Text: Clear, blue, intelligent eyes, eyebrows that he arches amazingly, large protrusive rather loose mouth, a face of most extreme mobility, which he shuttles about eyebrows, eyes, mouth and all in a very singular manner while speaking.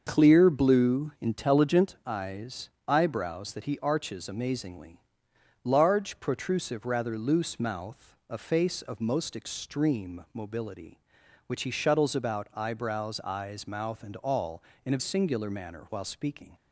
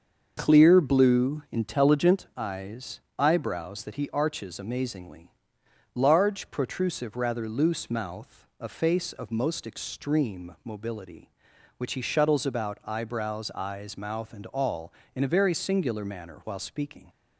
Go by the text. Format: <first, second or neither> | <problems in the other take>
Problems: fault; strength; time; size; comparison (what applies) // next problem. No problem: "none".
second | starts louder than the rest; until 1.0 s; 6.5 dB; also in the second // skips "very"; at 15.0 s